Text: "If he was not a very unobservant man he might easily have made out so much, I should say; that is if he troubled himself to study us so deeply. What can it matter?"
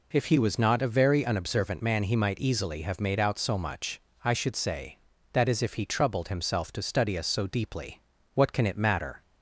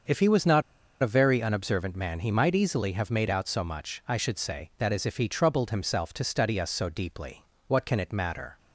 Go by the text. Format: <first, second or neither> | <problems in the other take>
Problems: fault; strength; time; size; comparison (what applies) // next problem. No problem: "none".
first | starts louder than the rest; until 1.4 s; 6.5 dB // pauses between "not" and "a"; at 0.6 s; 0.39 s long